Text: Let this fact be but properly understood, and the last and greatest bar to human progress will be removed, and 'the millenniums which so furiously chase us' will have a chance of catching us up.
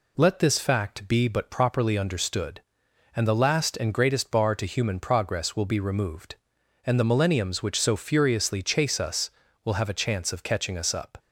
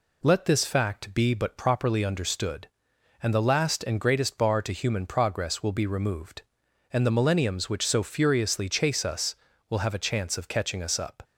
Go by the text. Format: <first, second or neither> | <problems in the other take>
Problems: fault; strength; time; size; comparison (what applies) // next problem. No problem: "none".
neither | none